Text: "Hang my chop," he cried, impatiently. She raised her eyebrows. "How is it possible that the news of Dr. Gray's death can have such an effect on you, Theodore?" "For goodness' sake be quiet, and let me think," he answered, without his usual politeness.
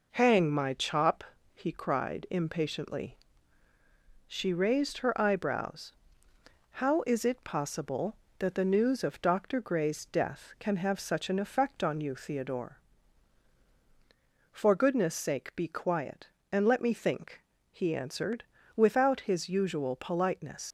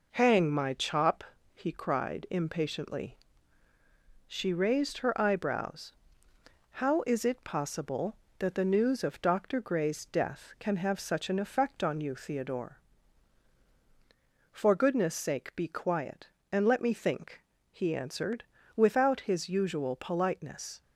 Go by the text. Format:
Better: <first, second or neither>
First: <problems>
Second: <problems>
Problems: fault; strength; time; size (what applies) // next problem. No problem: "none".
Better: second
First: leaves "politeness" unfinished; at 20.6 s; 110 ms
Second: none